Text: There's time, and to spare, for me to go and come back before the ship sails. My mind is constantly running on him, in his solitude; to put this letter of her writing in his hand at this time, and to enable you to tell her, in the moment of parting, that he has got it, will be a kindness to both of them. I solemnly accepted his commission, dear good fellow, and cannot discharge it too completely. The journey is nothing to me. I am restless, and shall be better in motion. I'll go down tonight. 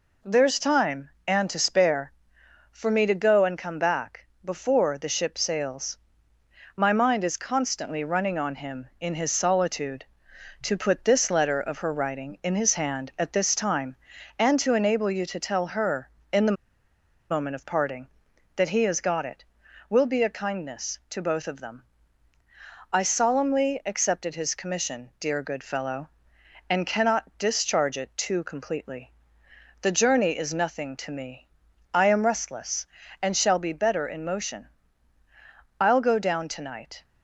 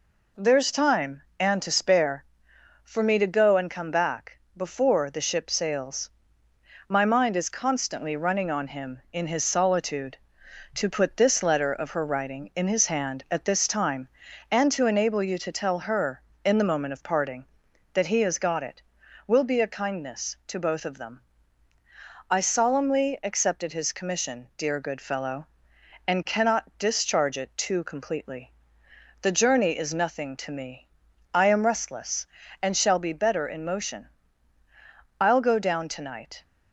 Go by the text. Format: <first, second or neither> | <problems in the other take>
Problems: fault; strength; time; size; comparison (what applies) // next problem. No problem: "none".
second | pauses between "back" and "before"; slight; at 4.2 s; 0.18 s long; slight in the second // pauses between "the" and "moment"; noticeable; at 16.5 s; 0.75 s long